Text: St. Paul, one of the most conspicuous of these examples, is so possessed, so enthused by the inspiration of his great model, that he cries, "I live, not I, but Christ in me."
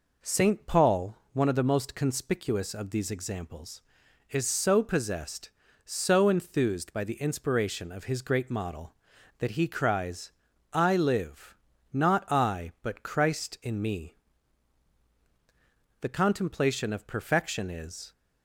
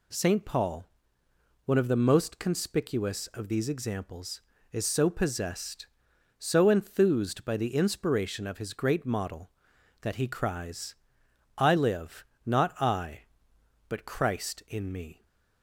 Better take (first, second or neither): second